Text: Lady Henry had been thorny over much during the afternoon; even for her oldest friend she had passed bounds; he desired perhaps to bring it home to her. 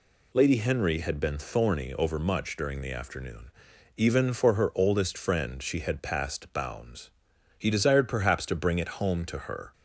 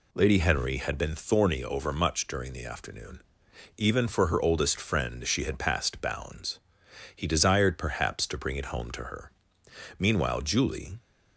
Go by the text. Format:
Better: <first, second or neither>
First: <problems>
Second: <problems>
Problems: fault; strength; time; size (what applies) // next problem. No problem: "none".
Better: first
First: none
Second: goes on to say "Meanwhile Julie"; noticeable; from 9.9 s on; 1.0 s long